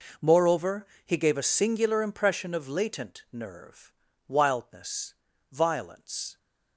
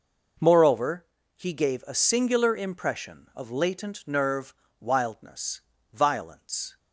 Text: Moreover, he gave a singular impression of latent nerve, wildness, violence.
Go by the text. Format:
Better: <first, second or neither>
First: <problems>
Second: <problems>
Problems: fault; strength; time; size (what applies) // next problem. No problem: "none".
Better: neither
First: none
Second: none